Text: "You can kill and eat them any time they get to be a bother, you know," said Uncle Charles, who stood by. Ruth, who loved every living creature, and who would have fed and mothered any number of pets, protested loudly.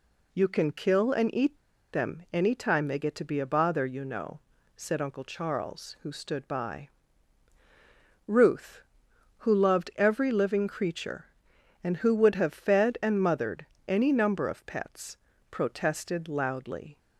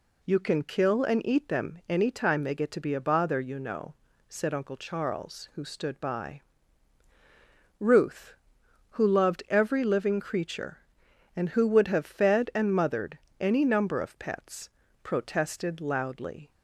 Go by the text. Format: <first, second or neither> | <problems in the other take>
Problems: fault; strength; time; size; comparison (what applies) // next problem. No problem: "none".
second | pauses between "eat" and "them"; at 1.5 s; 0.36 s long // pauses between "mothered" and "any"; slight; at 13.6 s; 0.22 s long; slight in the second